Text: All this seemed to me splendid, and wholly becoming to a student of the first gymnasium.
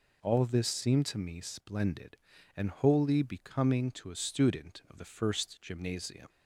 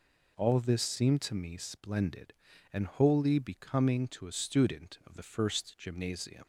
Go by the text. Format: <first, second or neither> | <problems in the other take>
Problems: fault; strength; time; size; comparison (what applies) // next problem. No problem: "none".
neither | none